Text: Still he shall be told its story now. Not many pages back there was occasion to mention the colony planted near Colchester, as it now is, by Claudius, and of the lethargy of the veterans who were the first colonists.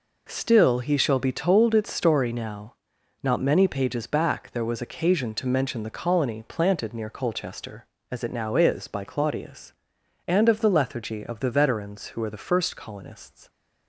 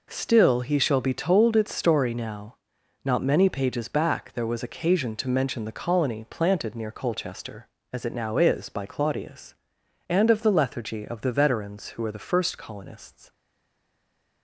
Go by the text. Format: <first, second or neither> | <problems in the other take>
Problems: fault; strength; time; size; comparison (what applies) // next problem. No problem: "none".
first | stays silent after the last word; from 13.3 s on; 1.1 s long